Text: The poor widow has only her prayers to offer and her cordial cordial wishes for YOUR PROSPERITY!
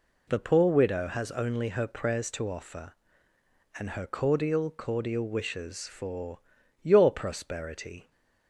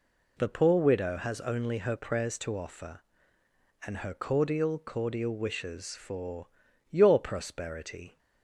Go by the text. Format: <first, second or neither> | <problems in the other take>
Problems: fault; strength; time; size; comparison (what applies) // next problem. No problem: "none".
neither | pauses between "for" and "YOUR"; the same in both